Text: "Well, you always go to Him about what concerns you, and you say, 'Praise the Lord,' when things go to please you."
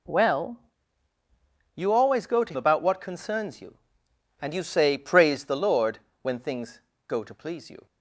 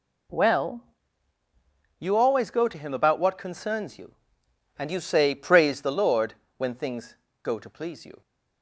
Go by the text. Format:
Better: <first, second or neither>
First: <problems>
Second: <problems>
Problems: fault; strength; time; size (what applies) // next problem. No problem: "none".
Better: second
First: skips "Him"; at 2.5 s // pauses between "things" and "go"; slight; at 6.8 s; 0.24 s long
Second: pauses between "things" and "go"; slight; at 7.1 s; 0.24 s long